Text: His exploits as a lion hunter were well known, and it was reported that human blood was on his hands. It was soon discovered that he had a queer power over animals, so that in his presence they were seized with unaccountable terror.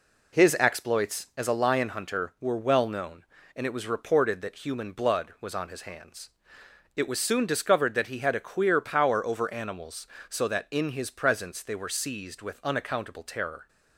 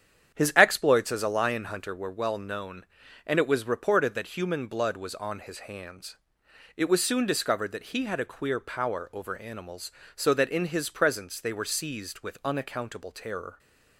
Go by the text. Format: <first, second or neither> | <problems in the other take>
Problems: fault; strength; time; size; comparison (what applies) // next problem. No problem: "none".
first | starts louder than the rest; strong; until 2.0 s; 9 dB